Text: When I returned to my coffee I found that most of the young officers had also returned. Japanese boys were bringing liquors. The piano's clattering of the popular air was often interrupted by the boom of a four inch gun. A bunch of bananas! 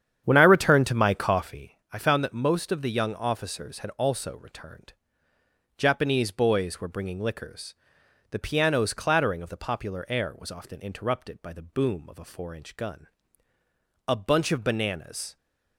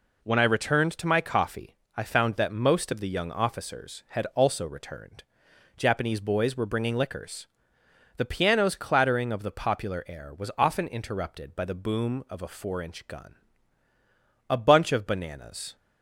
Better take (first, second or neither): second